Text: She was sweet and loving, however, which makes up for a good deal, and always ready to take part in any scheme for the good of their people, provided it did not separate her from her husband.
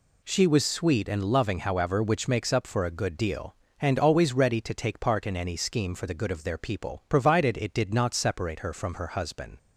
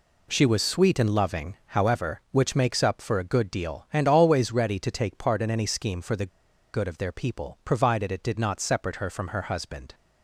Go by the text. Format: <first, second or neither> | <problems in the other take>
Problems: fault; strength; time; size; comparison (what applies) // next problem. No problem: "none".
first | pauses between "the" and "good"; at 6.2 s; 0.45 s long